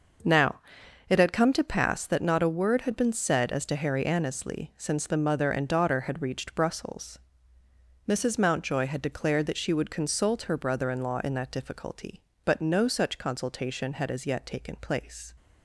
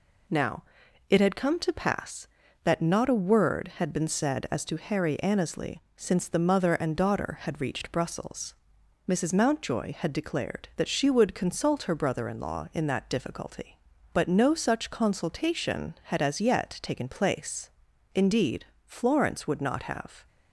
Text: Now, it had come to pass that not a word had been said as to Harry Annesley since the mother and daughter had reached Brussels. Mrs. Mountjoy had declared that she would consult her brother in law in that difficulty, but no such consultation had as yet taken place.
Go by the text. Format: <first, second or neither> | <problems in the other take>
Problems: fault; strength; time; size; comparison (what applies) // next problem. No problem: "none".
first | goes on to say "Indeed Florence would not have"; strong; from 18.1 s on; 2.1 s long